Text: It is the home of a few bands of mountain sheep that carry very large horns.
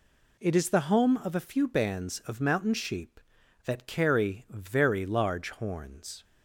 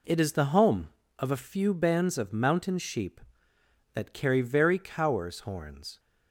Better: first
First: none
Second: says "cowers" for "large"; at 4.7 s

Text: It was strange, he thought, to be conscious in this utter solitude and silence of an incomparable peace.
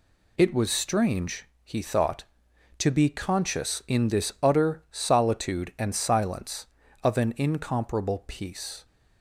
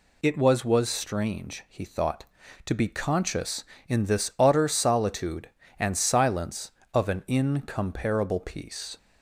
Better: first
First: none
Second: says "was" twice; at 0.6 s

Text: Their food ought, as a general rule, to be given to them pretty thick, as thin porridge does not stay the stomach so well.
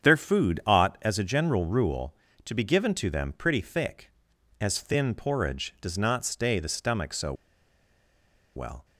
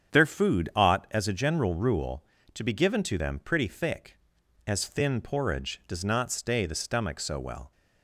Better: second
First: starts louder than the rest; strong; until 1.1 s; 7.5 dB // pauses between "so" and "well"; strong; at 7.3 s; 1.2 s long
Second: starts louder than the rest; strong; until 1.2 s; 8 dB

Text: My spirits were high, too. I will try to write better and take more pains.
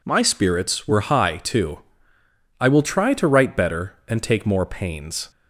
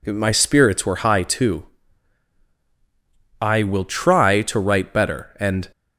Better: first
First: none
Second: stops before "take more pains"; at 5.7 s

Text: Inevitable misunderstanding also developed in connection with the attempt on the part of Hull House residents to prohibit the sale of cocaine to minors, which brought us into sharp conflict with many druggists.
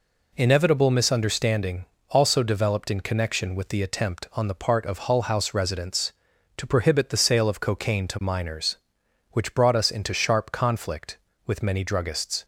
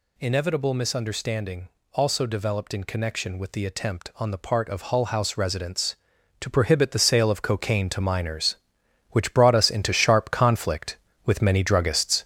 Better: first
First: pauses between "misunderstanding" and "also"; slight; at 1.8 s; 0.24 s long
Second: gets louder; throughout; 6.5 dB // pauses between "misunderstanding" and "also"; slight; at 1.6 s; 0.24 s long

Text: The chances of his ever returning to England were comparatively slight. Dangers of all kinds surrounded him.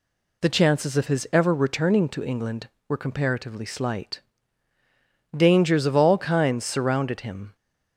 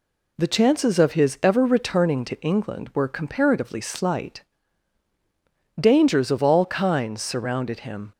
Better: neither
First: none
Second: none

